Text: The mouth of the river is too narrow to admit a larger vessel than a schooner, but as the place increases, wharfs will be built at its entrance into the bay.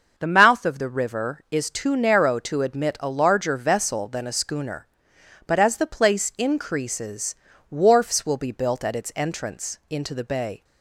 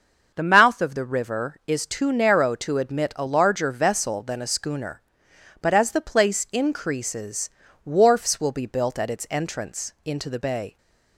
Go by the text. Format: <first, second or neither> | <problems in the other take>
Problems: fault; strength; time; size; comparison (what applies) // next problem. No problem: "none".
neither | starts louder than the rest; the same in both